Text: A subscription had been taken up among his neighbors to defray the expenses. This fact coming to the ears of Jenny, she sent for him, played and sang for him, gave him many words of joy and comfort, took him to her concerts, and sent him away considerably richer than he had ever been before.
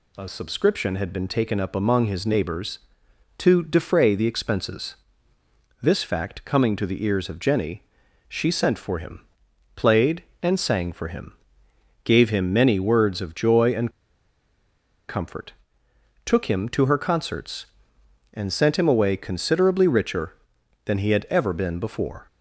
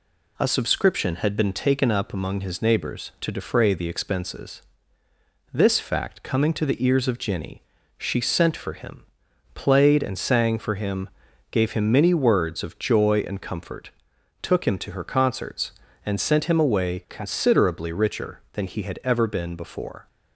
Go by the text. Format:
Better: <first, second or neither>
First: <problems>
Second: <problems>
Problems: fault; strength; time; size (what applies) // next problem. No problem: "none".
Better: second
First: pauses between "and" and "comfort"; at 13.8 s; 1.1 s long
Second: none